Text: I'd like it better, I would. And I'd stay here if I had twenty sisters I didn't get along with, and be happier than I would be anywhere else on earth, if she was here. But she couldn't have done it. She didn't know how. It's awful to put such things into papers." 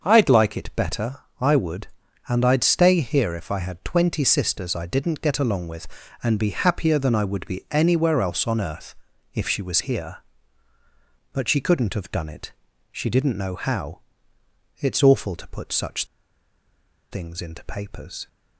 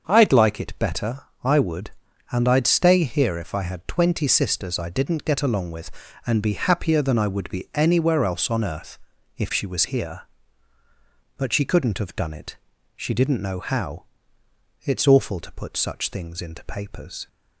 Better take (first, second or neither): second